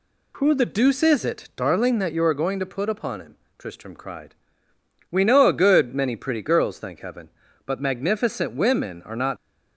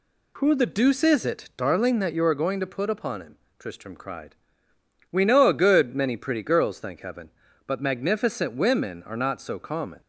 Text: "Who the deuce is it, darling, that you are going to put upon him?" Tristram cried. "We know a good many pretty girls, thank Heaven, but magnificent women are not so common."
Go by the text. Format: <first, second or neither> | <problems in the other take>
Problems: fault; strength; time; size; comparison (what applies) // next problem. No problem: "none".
second | stops before "so common"; at 9.3 s